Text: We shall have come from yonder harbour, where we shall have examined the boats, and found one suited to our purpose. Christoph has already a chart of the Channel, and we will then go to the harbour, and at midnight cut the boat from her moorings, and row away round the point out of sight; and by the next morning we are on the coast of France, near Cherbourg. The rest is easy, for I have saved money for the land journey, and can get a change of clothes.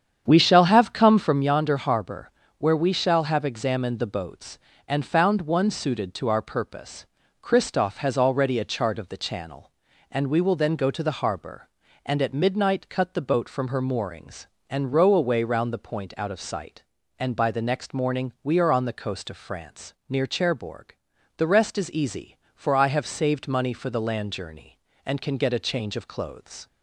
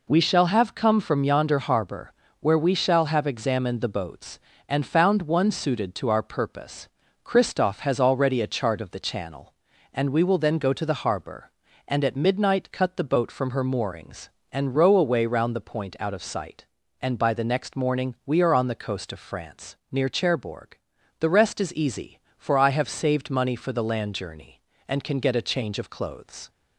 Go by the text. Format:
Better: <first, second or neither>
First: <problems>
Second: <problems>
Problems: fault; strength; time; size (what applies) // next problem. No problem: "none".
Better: second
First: starts louder than the rest; strong; until 1.4 s; 8.5 dB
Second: none